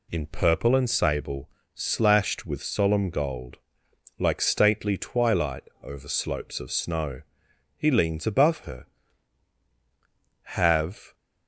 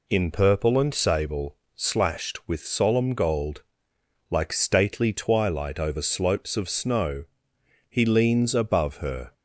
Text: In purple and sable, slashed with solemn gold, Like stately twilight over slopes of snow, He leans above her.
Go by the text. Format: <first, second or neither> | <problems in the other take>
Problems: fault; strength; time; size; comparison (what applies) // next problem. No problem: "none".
second | pauses between "twilight" and "over"; slight; at 5.6 s; 0.20 s long // goes on to say "Have"; noticeable; from 10.4 s on; 0.72 s long